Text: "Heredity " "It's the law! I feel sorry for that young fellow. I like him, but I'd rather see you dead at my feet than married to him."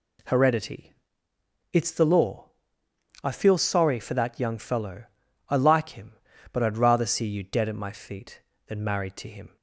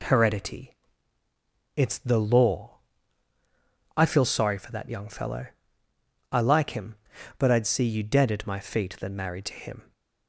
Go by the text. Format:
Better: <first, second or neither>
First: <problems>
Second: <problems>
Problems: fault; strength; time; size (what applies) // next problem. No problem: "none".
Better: first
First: none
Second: skips "rather"; at 7.6 s